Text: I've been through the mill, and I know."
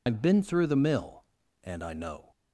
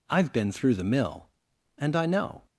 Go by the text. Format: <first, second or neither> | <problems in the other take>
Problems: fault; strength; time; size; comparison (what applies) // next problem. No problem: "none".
second | loses the start of "I've"; at 0.0 s; 95 ms